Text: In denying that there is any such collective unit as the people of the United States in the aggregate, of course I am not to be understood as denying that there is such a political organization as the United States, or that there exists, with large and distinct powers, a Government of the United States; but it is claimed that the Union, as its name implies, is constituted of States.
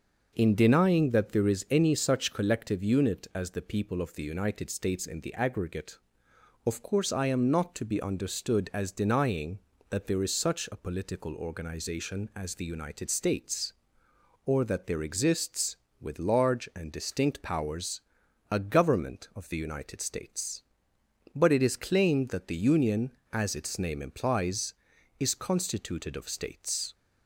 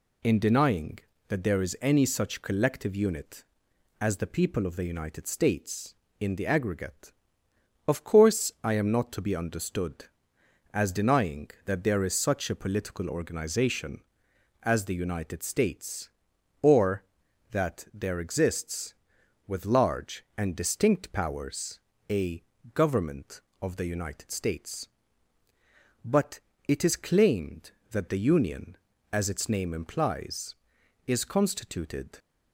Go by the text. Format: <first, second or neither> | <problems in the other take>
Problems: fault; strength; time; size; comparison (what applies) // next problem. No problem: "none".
first | pauses between "a" and "Government"; slight; at 22.4 s; 0.32 s long // pauses between "but" and "it"; slight; at 26.4 s; 0.26 s long // stops before "of States"; at 32.1 s